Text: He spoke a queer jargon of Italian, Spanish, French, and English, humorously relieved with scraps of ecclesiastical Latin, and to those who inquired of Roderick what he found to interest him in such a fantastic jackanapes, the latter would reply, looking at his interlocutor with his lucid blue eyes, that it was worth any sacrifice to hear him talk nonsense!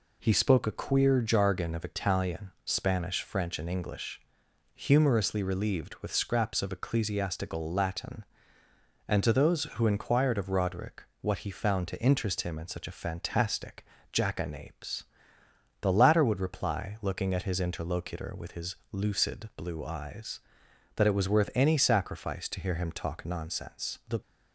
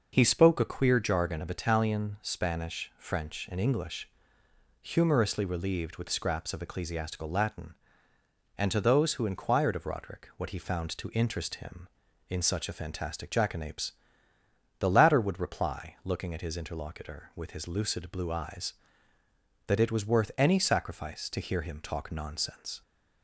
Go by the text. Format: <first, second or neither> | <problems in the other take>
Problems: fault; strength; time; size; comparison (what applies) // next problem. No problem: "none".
second | pauses between "Roderick" and "what"; slight; at 11.0 s; 0.20 s long // pauses between "fantastic" and "jackanapes"; slight; at 13.8 s; 0.30 s long // pauses between "his" and "lucid"; slight; at 18.7 s; 0.16 s long // goes on to say "The"; slight; from 24.0 s on; 0.14 s long